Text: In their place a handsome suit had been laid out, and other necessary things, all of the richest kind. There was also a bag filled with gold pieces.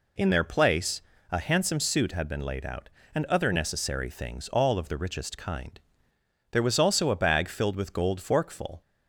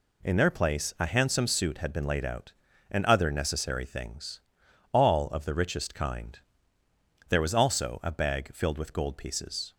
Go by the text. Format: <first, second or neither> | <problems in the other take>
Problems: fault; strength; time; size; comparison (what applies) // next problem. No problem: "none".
second | pauses between "place" and "a"; slight; at 1.0 s; 0.28 s long // says "forkful" for "pieces"; at 8.1 s